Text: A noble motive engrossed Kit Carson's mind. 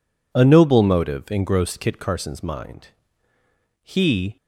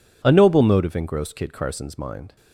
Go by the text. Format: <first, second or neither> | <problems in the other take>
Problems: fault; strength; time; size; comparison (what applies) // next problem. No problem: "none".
second | goes on to say "He"; from 3.8 s on; 0.54 s long